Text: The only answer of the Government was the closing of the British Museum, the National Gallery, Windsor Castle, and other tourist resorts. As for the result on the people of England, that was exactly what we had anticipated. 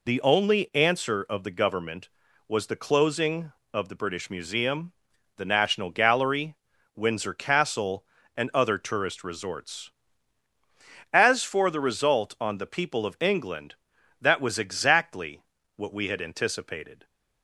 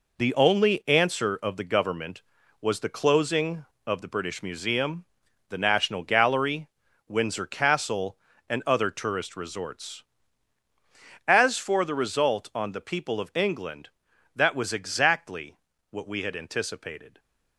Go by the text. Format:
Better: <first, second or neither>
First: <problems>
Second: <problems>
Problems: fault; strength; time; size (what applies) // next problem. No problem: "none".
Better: first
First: pauses between "exactly" and "what"; slight; at 15.4 s; 0.34 s long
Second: gets quieter; strong; throughout; 8 dB // pauses between "exactly" and "what"; slight; at 15.5 s; 0.34 s long